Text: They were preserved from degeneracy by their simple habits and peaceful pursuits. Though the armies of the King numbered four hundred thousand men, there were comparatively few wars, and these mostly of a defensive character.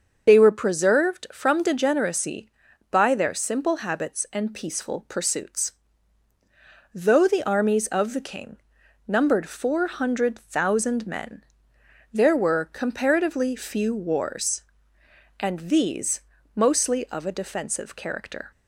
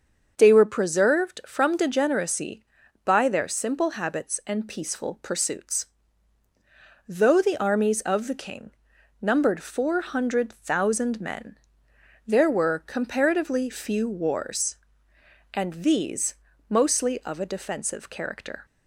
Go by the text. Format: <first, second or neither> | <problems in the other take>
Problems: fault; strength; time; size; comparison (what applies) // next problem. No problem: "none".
second | loses the start of "They"; at 0.2 s; 45 ms // starts louder than the rest; until 1.3 s; 6.5 dB; also in the second // pauses between "King" and "numbered"; noticeable; at 8.5 s; 0.50 s long; noticeable in the second // pauses between "these" and "mostly"; slight; at 16.2 s; 0.34 s long; slight in the second